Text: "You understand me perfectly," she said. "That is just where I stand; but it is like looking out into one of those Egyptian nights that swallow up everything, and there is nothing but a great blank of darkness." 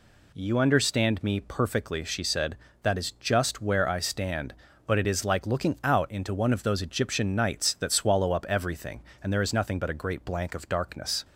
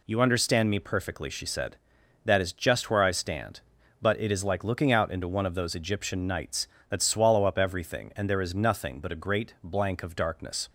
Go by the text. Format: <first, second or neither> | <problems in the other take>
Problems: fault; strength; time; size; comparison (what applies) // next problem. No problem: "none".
neither | none